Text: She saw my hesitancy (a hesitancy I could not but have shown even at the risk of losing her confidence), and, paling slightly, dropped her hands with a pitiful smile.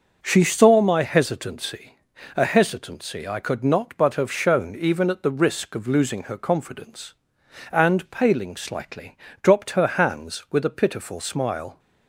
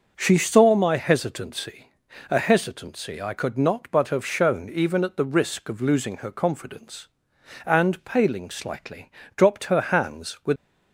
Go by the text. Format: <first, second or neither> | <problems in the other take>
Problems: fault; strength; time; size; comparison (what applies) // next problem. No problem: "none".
first | starts louder than the rest; until 1.1 s; 6 dB; also in the first // stops before "a pitiful smile"; at 10.5 s